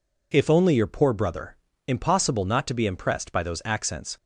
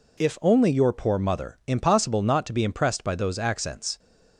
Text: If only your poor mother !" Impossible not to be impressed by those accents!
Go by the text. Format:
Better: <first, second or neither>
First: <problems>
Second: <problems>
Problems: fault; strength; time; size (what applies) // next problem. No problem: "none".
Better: second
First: says "brother" for "mother"; at 1.1 s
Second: none